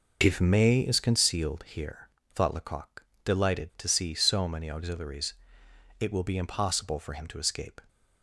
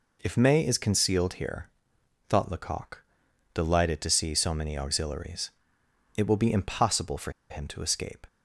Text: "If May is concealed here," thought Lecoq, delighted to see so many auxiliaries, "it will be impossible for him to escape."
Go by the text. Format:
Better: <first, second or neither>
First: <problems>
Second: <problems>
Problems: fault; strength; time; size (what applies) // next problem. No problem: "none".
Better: first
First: none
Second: pauses between "for" and "him"; slight; at 7.3 s; 0.19 s long